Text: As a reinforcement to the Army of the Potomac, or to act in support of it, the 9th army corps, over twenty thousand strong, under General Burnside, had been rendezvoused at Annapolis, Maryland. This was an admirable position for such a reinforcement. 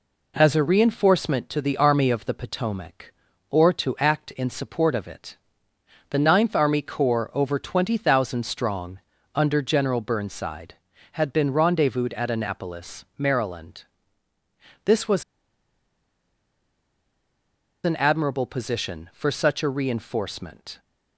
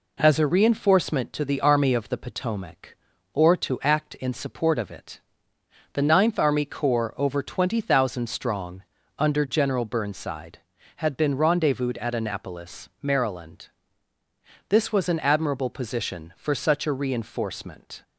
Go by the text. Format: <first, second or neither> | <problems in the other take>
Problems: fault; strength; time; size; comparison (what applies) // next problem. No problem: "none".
second | pauses between "was" and "an"; strong; at 15.2 s; 2.6 s long